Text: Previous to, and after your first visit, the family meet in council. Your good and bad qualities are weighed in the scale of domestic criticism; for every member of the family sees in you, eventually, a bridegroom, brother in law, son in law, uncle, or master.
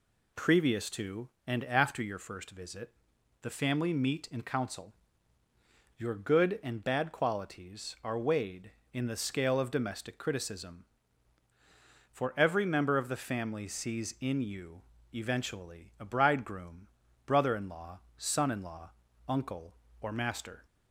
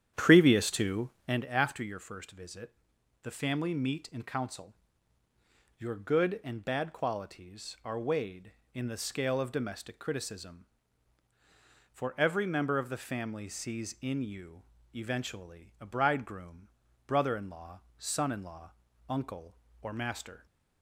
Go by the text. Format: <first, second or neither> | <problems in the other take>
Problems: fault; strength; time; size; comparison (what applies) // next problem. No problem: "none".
first | starts louder than the rest; strong; until 1.4 s; 9.5 dB